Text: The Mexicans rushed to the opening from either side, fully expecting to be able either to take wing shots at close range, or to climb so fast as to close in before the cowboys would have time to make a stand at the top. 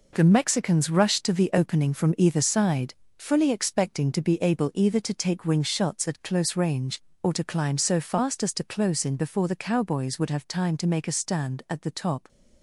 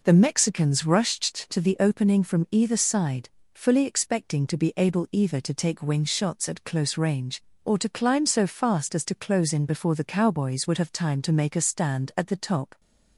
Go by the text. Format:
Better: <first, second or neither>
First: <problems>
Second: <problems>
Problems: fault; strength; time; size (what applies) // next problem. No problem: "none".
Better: second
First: gets quieter; strong; throughout; 8.5 dB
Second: none